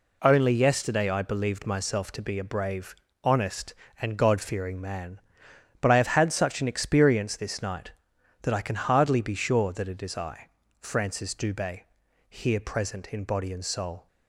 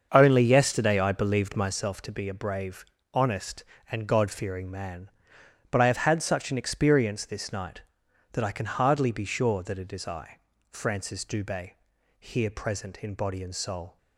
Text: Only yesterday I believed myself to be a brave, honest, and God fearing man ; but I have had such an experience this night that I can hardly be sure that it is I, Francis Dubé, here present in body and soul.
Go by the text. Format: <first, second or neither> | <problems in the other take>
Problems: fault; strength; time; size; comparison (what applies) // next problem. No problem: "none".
first | starts louder than the rest; until 1.8 s; 6.5 dB